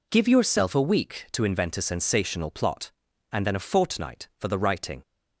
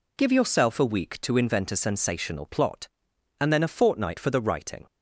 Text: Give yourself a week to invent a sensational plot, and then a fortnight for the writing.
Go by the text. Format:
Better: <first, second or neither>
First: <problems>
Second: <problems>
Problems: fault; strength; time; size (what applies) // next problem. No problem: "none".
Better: neither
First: none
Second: none